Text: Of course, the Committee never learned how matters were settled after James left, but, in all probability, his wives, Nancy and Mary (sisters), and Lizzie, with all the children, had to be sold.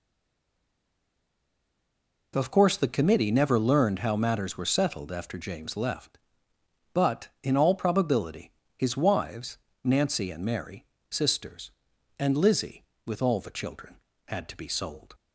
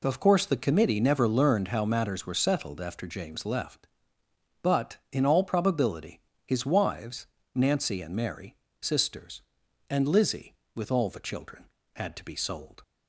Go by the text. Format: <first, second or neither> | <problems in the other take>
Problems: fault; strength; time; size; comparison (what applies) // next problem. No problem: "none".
second | stays silent before the first word; until 2.3 s; 2.3 s long